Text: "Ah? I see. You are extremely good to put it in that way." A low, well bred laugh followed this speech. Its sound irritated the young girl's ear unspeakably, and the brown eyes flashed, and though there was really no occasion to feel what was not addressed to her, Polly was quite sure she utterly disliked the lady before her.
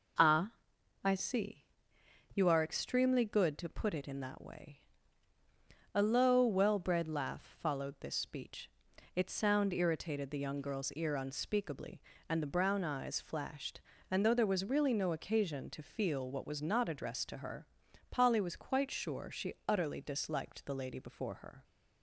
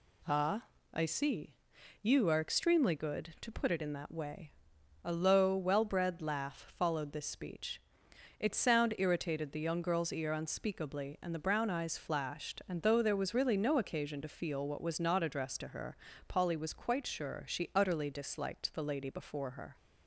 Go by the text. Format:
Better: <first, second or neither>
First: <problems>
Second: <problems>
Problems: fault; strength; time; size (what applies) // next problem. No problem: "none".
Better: neither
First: none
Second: none